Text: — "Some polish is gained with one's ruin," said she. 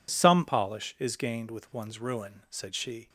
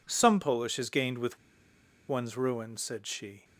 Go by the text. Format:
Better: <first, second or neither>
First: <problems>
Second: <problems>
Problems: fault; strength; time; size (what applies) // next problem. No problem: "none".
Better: first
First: none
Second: pauses between "with" and "one's"; noticeable; at 1.3 s; 0.71 s long